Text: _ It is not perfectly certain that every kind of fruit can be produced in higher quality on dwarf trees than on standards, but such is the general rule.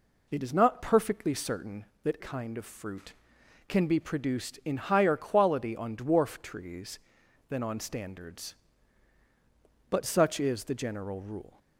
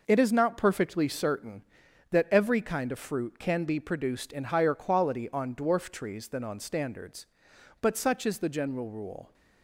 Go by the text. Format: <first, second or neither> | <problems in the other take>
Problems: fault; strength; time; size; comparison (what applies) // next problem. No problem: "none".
second | skips "every"; at 2.1 s